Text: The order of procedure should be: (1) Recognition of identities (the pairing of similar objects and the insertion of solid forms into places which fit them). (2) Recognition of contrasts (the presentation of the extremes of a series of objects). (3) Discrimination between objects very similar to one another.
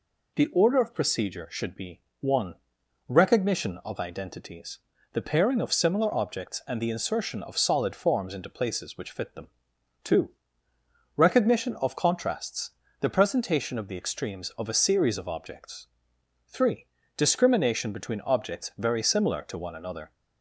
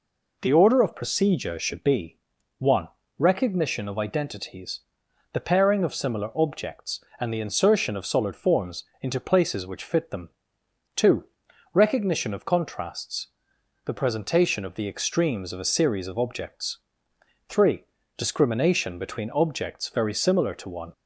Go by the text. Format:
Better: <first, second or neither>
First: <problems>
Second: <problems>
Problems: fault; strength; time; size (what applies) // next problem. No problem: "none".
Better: first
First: none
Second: pauses between "forms" and "into"; slight; at 8.8 s; 0.16 s long // stops before "another"; at 20.9 s